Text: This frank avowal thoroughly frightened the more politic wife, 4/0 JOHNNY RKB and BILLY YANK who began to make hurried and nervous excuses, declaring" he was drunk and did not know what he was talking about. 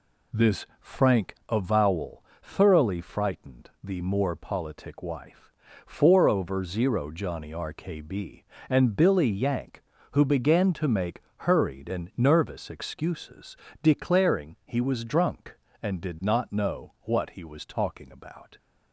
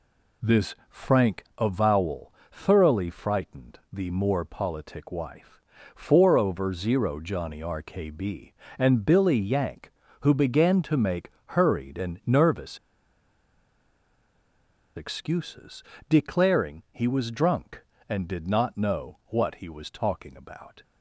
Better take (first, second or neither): first